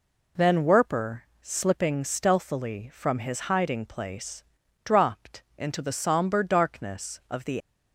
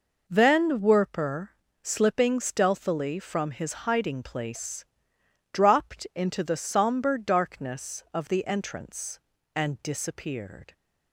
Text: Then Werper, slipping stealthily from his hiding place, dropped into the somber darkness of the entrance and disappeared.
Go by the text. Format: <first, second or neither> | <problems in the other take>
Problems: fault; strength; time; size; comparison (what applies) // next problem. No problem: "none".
second | stops before "entrance and disappeared"; at 7.6 s